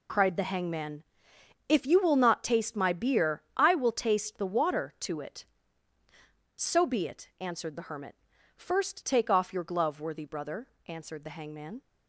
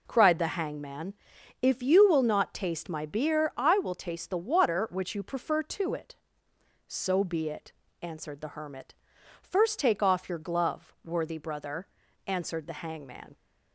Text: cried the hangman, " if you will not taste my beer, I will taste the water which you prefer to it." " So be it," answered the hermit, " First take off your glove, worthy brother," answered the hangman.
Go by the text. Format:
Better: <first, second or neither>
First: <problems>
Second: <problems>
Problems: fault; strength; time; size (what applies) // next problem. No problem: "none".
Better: second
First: skips "which you prefer"; at 4.9 s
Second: none